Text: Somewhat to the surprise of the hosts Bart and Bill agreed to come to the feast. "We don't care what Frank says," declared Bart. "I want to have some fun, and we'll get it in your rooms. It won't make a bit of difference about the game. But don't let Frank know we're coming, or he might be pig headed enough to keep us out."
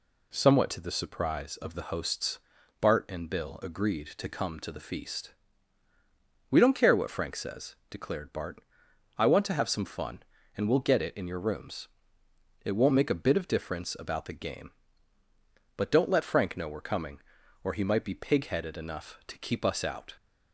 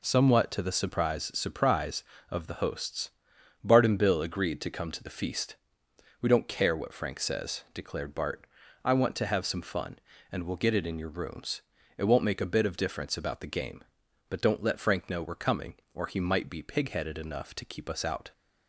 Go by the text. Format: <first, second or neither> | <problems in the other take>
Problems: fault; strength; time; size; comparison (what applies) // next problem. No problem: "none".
first | says "surprise" twice; at 1.3 s // pauses between "hosts" and "Bart"; noticeable; at 3.1 s; 0.52 s long; also in the first